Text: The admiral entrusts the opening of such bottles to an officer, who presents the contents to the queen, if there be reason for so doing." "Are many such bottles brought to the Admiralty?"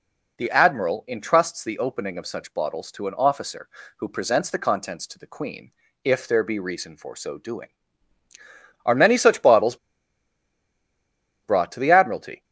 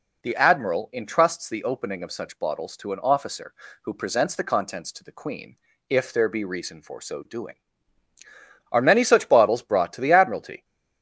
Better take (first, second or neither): second